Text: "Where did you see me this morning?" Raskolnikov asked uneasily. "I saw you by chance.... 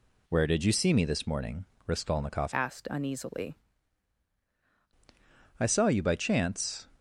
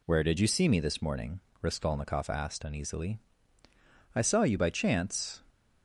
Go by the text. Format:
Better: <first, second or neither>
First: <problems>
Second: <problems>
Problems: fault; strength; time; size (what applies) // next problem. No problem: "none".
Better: second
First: changes voice from "asked" to "uneasily"; from 2.5 to 3.5 s; 1.0 s long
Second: none